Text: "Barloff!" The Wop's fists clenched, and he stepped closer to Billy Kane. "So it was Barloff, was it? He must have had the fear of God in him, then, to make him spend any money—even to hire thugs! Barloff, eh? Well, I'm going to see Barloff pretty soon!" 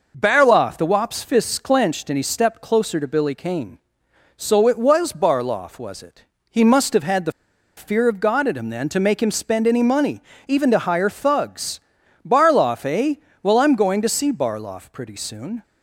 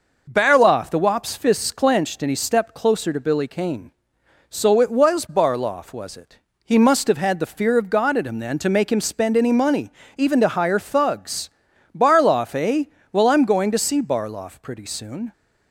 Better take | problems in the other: second | pauses between "the" and "fear"; noticeable; at 7.3 s; 0.45 s long

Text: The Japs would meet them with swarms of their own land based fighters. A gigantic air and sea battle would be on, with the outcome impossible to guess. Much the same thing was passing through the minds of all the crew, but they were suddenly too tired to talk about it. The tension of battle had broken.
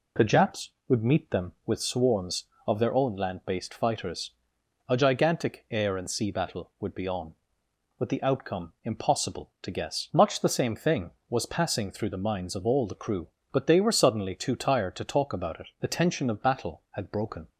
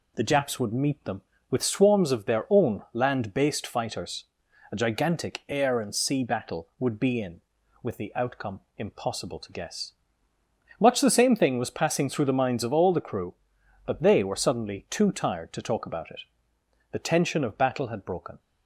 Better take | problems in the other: first | says "in" for "on"; at 7.1 s // pauses between "outcome" and "impossible"; slight; at 8.5 s; 0.18 s long

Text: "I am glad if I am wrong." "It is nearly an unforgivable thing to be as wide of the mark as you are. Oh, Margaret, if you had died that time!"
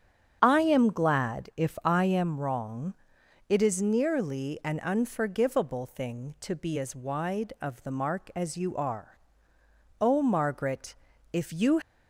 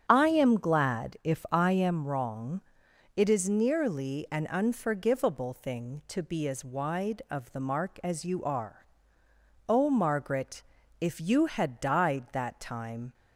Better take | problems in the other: second | starts louder than the rest; strong; until 1.4 s; 8 dB; strong in the second // stops before "had died that time"; at 11.8 s

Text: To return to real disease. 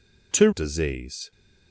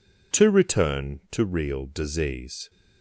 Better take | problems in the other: second | skips "return to real"; at 0.5 s

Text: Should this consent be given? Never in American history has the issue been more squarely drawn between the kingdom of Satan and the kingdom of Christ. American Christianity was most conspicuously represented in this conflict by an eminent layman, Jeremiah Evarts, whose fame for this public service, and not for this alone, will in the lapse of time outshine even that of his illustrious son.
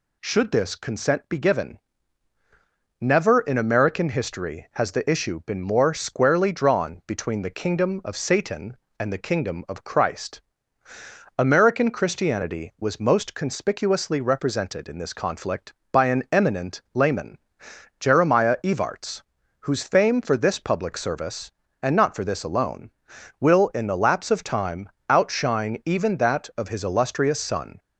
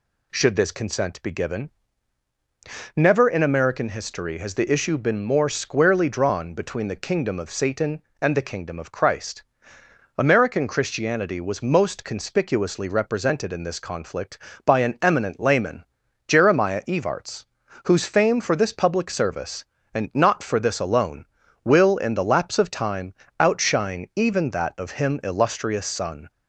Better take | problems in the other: first | pauses between "time" and "outshine"; slight; at 23.1 s; 0.24 s long; slight in the first // says "him" for "his"; at 24.9 s

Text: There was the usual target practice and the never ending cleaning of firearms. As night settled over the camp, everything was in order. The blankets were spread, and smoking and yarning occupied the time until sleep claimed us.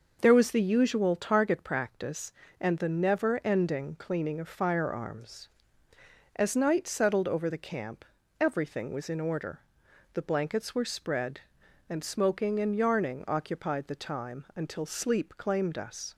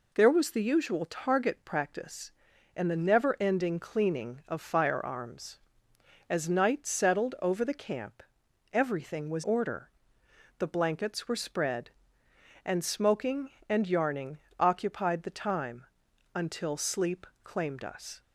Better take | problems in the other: first | skips "in"; at 9.4 s // pauses between "yarning" and "occupied"; slight; at 14.3 s; 0.22 s long // pauses between "time" and "until"; noticeable; at 15.8 s; 0.50 s long // pauses between "sleep" and "claimed"; slight; at 17.2 s; 0.18 s long

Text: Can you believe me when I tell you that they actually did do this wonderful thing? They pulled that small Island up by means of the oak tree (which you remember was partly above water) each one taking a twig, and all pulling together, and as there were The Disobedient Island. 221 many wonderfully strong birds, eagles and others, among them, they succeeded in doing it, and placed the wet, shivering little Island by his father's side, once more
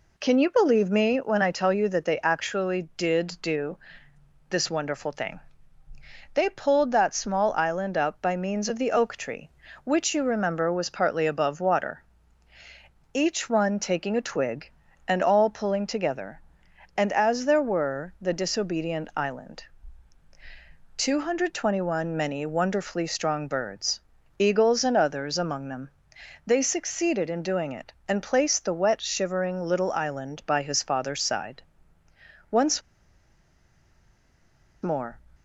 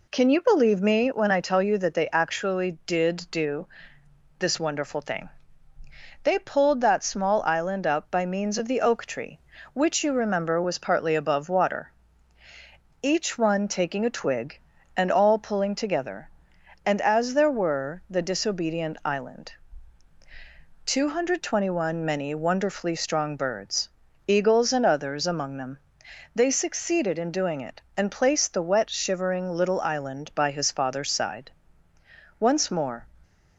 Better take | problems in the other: second | pauses between "do" and "this"; noticeable; at 3.7 s; 0.70 s long; noticeable in the second // pauses between "once" and "more"; strong; at 32.8 s; 2.0 s long

